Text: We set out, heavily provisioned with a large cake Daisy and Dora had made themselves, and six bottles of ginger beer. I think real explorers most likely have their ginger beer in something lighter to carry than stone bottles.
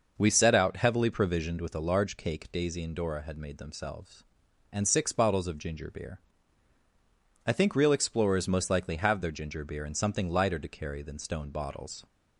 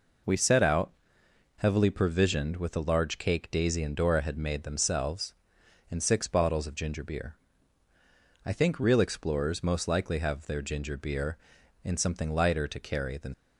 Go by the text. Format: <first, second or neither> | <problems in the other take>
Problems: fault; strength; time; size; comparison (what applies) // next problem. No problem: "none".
first | stops before "stone bottles"; at 13.3 s